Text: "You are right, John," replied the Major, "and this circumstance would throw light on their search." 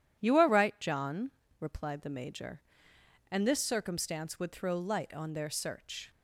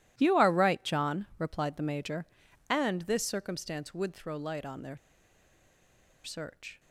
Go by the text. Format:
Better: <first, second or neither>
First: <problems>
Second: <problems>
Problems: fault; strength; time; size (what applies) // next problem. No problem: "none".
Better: first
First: none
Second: pauses between "their" and "search"; strong; at 4.9 s; 1.2 s long